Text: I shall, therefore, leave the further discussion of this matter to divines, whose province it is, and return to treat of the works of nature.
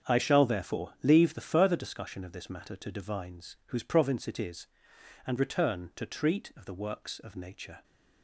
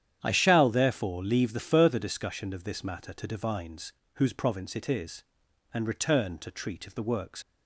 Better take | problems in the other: first | starts louder than the rest; strong; until 1.2 s; 9.5 dB; also in the first // stops before "of nature"; at 7.4 s

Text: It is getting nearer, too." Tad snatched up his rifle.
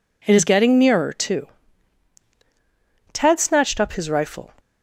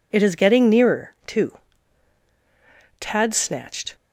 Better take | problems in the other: first | stops before "up his rifle"; at 3.9 s

